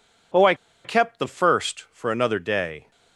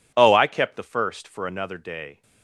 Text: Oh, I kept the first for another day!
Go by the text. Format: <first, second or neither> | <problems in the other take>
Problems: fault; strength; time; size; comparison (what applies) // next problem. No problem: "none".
second | pauses between "I" and "kept"; slight; at 0.5 s; 0.29 s long